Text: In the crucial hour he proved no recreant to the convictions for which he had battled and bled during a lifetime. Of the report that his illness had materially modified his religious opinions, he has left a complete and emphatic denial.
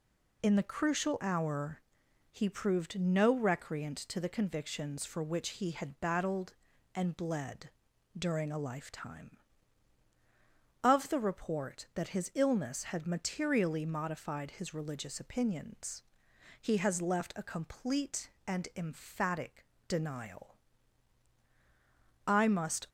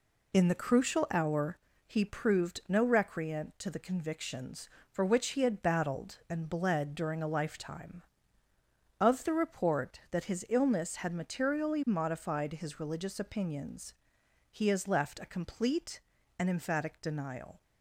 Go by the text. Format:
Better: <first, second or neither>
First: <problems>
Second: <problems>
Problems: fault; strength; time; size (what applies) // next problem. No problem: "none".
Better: second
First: pauses between "hour" and "he"; noticeable; at 1.8 s; 0.50 s long // pauses between "bled" and "during"; noticeable; at 7.7 s; 0.48 s long // pauses between "emphatic" and "denial"; slight; at 19.6 s; 0.22 s long // goes on to say "I must"; noticeable; from 22.2 s on; 0.62 s long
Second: pauses between "hour" and "he"; slight; at 1.5 s; 0.30 s long